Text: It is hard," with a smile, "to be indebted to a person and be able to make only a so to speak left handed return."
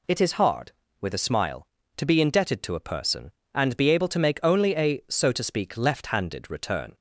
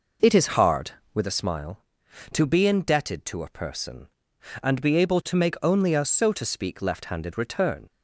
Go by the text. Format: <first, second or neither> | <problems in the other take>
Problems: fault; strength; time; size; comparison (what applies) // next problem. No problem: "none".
first | starts louder than the rest; noticeable; until 1.3 s; 5 dB